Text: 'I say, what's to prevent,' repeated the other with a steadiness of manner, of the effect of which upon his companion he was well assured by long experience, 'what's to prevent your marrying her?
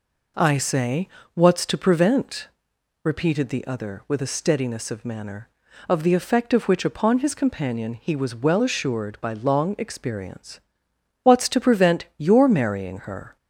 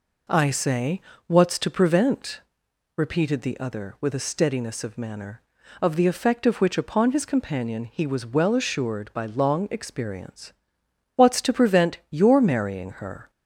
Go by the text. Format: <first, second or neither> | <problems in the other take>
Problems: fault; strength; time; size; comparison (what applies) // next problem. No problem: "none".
neither | none